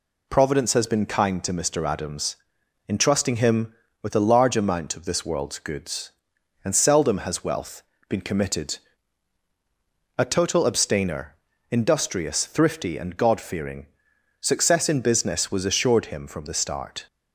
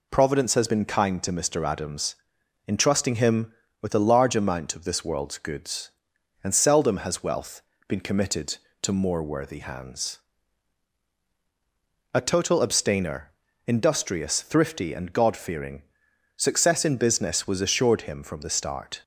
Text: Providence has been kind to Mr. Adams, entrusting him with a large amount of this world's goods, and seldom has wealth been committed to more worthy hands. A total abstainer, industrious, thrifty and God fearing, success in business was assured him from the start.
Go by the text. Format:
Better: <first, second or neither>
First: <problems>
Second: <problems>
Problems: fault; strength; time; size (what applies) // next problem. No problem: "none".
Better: second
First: pauses between "wealth" and "been"; slight; at 7.8 s; 0.26 s long // skips "to more worthy hands"; at 9.4 s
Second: pauses between "wealth" and "been"; slight; at 7.6 s; 0.26 s long